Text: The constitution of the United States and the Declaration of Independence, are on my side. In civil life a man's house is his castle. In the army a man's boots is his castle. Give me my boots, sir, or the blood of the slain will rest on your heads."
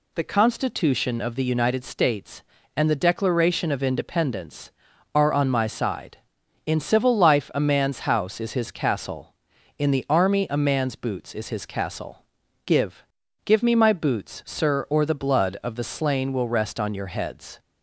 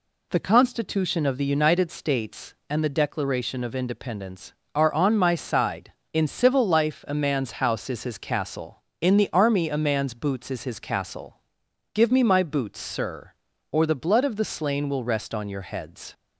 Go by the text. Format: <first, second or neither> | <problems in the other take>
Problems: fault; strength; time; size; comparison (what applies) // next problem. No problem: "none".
second | says "Give" twice; at 13.4 s